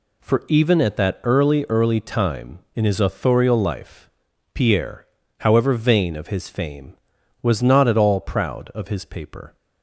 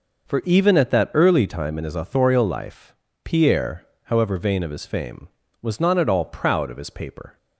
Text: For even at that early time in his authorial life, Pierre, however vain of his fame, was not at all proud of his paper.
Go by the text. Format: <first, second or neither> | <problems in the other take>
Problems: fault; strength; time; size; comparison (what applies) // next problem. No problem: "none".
second | says "early" twice; at 1.6 s